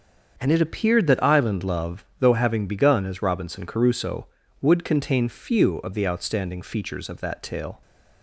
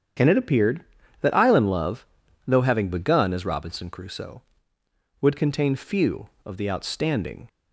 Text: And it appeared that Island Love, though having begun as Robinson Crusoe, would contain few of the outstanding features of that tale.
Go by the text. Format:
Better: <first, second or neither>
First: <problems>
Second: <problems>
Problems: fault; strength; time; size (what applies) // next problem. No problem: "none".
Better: first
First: starts louder than the rest; until 1.4 s; 7 dB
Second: starts louder than the rest; strong; until 1.5 s; 8.5 dB // stops before "features of that tale"; at 7.4 s